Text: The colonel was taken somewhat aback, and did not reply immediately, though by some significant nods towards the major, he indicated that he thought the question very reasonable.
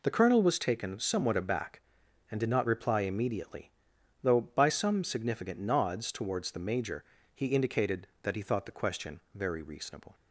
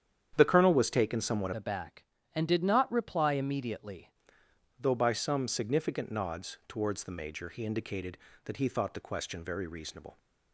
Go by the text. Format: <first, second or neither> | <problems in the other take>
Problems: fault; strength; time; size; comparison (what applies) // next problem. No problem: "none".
first | starts louder than the rest; strong; until 1.3 s; 9 dB // changes voice from "aback" to "immediately"; from 1.5 to 4.1 s; 2.6 s long